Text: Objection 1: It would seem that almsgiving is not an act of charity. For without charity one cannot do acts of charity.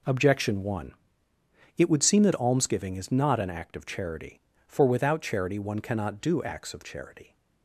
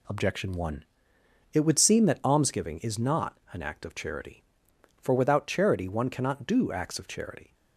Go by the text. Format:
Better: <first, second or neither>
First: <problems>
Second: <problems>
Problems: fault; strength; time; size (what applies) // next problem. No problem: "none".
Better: neither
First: none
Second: none